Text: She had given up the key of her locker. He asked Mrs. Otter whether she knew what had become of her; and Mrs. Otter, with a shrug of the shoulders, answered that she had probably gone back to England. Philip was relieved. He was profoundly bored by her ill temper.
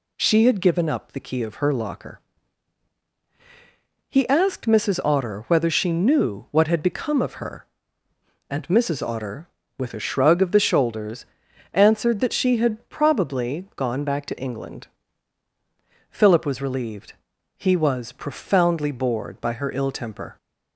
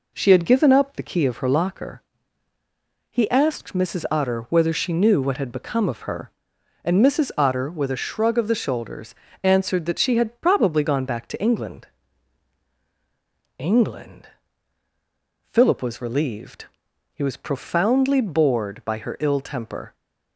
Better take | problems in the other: first | says "England" twice; at 13.5 s

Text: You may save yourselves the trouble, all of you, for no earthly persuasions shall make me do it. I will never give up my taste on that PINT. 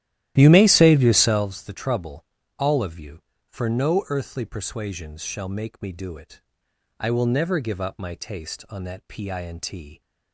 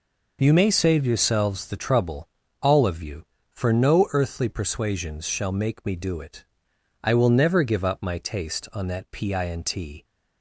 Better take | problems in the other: second | starts louder than the rest; strong; until 1.5 s; 13.5 dB

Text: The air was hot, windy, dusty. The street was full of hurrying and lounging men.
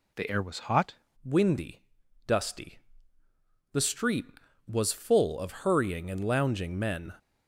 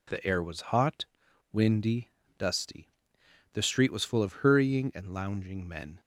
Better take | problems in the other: second | changes voice at "windy"; from 1.2 s on; 5.9 s long

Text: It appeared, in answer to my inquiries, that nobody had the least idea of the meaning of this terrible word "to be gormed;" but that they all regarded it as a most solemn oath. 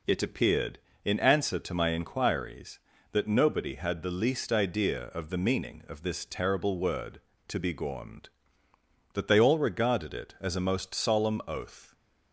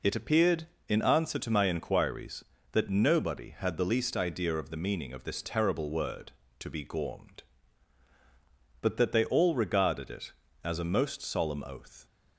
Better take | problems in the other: second | skips "but"; at 8.7 s

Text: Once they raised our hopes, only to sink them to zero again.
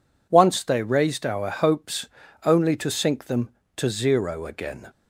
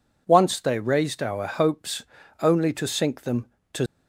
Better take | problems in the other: first | stops before "zero again"; at 3.8 s

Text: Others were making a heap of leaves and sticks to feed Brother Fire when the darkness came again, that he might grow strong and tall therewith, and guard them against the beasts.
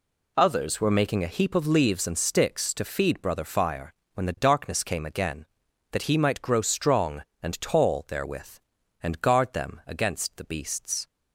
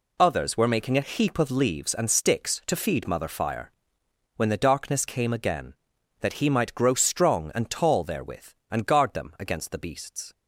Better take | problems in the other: first | says "Mother" for "Brother"; at 3.0 s // pauses between "Fire" and "when"; noticeable; at 3.7 s; 0.64 s long; slight in the first

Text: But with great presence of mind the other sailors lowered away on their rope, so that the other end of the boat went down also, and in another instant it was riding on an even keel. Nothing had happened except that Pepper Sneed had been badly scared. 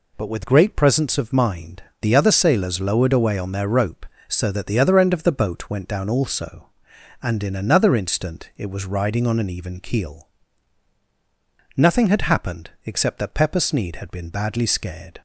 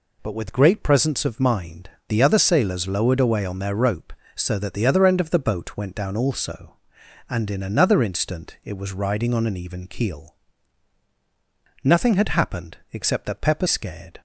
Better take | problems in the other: first | pauses between "mind" and "the"; slight; at 1.9 s; 0.18 s long; slight in the first // skips "Sneed had been badly"; at 13.6 s

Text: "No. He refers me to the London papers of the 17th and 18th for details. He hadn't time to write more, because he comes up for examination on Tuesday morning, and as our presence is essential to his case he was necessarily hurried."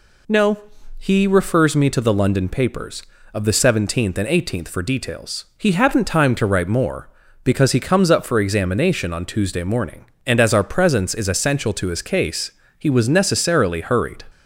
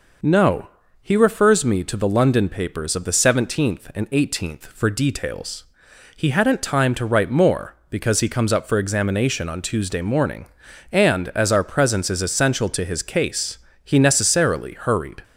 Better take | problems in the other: first | pauses between "case" and "he"; slight; at 13.5 s; 0.26 s long; slight in the first // skips "was"; at 13.9 s

